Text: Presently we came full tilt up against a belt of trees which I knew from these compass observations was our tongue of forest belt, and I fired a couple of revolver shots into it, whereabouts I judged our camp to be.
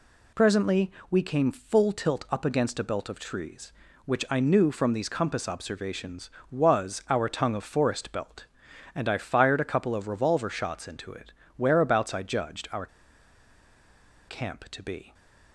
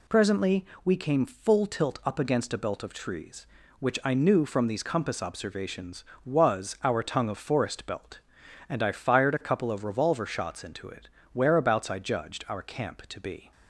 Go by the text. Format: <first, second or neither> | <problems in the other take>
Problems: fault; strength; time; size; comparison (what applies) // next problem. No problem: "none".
second | pauses between "Presently" and "we"; slight; at 0.9 s; 0.18 s long; slight in the second // pauses between "our" and "camp"; strong; at 12.8 s; 1.4 s long // stays silent after the last word; slight; from 15.0 s on; 0.5 s long